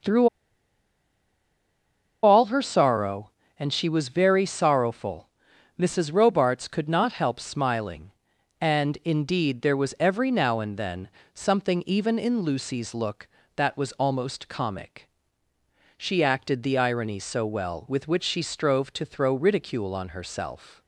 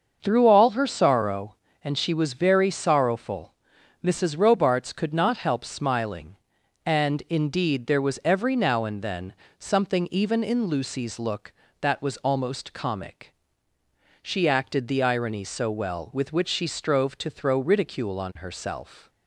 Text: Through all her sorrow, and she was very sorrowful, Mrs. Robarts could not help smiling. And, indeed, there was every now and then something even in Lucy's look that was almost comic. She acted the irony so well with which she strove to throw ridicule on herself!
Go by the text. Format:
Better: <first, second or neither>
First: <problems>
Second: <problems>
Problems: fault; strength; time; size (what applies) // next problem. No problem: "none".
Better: second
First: starts louder than the rest; until 2.9 s; 6 dB // pauses between "Through" and "all"; strong; at 0.2 s; 1.9 s long // pauses between "then" and "something"; slight; at 11.0 s; 0.26 s long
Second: starts louder than the rest; until 1.2 s; 6.5 dB // pauses between "then" and "something"; slight; at 9.3 s; 0.26 s long